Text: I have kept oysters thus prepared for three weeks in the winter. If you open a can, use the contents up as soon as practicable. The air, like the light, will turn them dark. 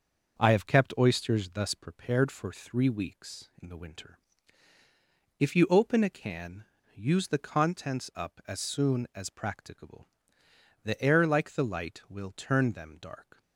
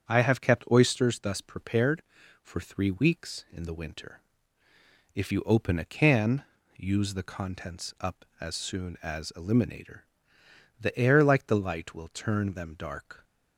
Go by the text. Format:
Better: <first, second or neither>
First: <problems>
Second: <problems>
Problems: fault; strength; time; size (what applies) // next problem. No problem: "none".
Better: first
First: none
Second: starts louder than the rest; strong; until 1.1 s; 7.5 dB // says "eliminator" for "practicable"; at 9.3 s